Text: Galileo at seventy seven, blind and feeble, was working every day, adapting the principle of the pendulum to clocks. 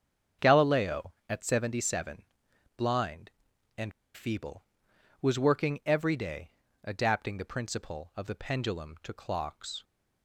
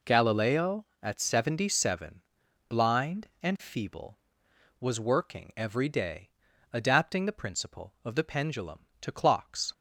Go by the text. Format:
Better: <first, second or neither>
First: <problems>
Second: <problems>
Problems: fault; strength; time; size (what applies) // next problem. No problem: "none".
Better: second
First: starts louder than the rest; strong; until 1.5 s; 7.5 dB // pauses between "and" and "feeble"; slight; at 3.9 s; 0.23 s long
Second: none